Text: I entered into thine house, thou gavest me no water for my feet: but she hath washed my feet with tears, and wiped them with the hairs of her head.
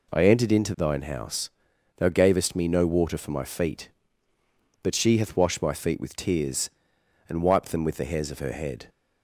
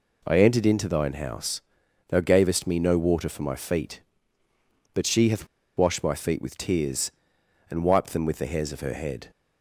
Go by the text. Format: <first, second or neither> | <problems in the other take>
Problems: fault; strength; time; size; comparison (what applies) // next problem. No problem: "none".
first | pauses between "hath" and "washed"; slight; at 5.4 s; 0.31 s long